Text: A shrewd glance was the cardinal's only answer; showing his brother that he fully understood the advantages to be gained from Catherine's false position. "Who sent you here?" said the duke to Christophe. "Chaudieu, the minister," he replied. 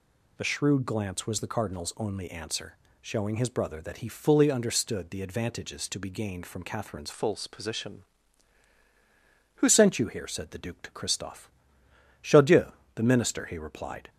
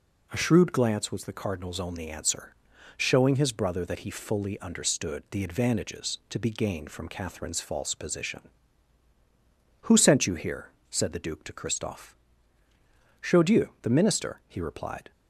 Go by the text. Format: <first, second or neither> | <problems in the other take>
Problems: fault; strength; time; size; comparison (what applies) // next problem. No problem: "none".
second | changes voice from "false" to "Who"; from 7.1 to 9.6 s; 2.5 s long